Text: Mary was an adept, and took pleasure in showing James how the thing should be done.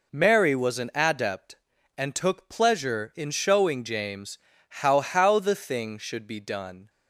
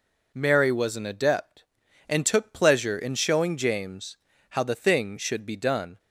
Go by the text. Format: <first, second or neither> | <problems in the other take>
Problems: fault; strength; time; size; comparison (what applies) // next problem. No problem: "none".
second | pauses between "James" and "how"; slight; at 4.3 s; 0.28 s long; slight in the second // says "how" twice; at 5.0 s